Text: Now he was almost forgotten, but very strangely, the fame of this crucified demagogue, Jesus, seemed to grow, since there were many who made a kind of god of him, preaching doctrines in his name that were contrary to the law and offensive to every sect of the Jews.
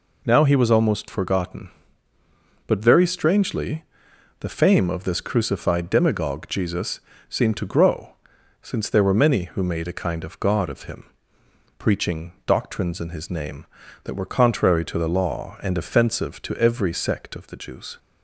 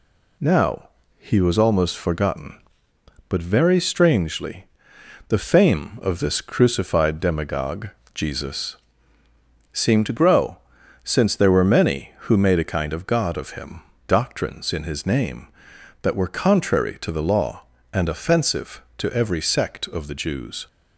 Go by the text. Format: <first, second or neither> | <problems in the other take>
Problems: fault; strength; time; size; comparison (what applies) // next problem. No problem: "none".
first | pauses between "Now" and "he"; slight; at 0.8 s; 0.28 s long // skips "preaching"; at 13.9 s